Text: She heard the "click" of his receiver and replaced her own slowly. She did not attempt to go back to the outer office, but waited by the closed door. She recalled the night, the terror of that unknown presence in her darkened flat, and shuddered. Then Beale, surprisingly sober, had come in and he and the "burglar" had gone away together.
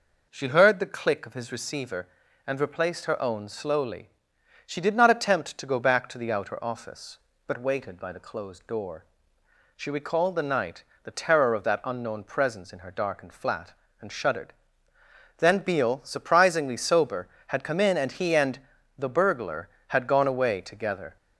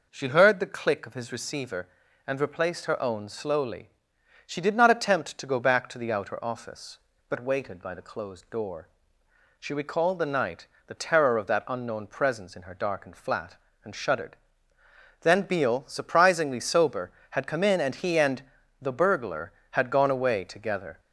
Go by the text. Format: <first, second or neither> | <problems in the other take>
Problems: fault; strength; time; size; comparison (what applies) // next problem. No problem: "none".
neither | pauses between "and" and "the"; the same in both